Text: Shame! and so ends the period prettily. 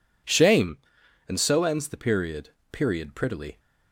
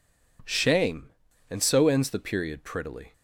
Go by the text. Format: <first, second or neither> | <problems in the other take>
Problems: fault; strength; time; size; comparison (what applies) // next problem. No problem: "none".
second | says "period" twice; at 2.7 s